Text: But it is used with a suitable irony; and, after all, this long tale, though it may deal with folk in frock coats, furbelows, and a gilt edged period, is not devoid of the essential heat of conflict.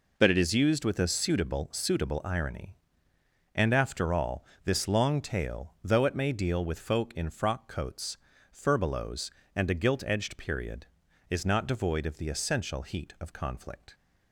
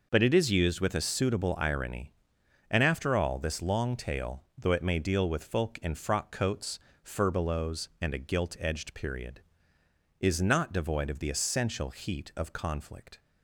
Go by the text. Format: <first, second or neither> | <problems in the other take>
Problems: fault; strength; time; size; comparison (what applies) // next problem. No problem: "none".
second | says "suitable" twice; at 1.7 s